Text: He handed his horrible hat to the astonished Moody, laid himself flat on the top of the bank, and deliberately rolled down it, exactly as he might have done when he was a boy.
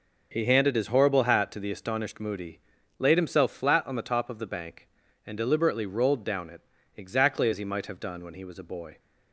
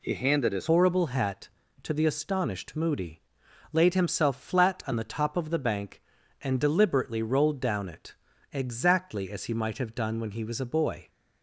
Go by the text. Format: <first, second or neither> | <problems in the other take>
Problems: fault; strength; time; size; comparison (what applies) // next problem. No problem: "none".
first | changes voice at "horrible"; from 0.7 s on; 10.3 s long